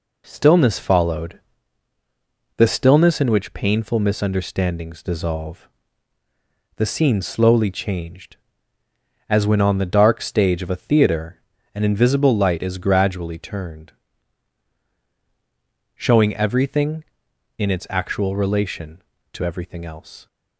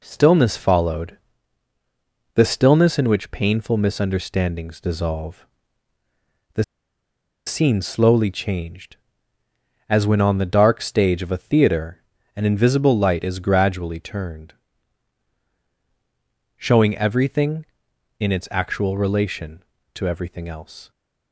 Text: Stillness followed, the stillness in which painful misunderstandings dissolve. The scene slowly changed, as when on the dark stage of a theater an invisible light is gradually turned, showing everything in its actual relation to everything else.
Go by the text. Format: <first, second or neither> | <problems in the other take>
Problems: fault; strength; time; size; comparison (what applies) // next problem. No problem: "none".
first | pauses between "The" and "scene"; noticeable; at 6.6 s; 0.82 s long // pauses between "theater" and "an"; slight; at 12.0 s; 0.34 s long; slight in the first